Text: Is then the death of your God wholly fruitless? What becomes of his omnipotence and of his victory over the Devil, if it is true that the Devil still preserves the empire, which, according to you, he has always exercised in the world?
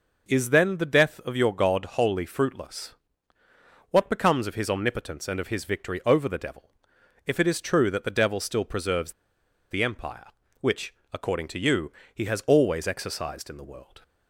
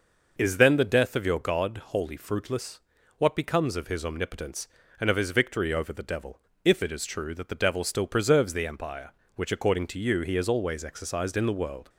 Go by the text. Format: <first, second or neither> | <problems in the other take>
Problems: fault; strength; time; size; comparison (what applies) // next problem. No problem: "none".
second | pauses between "preserves" and "the"; noticeable; at 9.1 s; 0.57 s long